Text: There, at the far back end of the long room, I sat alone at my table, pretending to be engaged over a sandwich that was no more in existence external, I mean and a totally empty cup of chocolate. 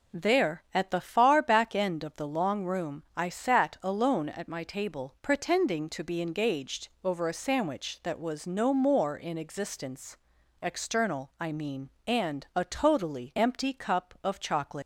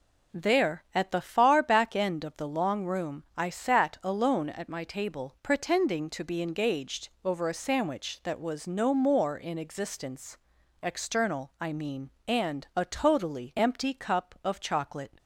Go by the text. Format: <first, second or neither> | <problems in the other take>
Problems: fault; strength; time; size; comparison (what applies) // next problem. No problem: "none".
second | pauses between "engaged" and "over"; slight; at 6.8 s; 0.16 s long; slight in the second // pauses between "existence" and "external"; noticeable; at 10.1 s; 0.48 s long; noticeable in the second // leaves "chocolate" unfinished; at 14.8 s; 150 ms